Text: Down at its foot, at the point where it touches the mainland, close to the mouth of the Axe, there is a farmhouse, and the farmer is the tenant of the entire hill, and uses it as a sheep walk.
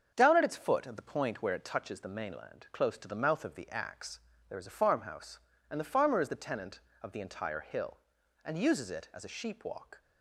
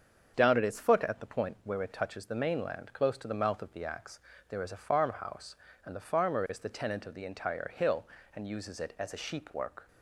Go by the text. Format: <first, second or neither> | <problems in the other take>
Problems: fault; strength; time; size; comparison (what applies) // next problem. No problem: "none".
first | starts louder than the rest; until 1.3 s; 7 dB; also in the first // says "work" for "walk"; at 9.5 s